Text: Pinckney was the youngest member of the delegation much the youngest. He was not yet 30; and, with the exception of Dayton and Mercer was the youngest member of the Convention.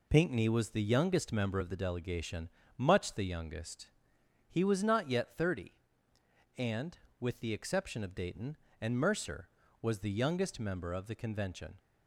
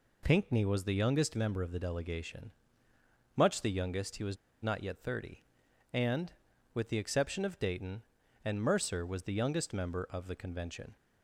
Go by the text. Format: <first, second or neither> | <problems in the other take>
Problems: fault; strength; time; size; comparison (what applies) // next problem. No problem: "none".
first | pauses between "delegation" and "much"; noticeable; at 2.4 s; 0.86 s long; slight in the first // pauses between "was" and "not"; slight; at 4.3 s; 0.27 s long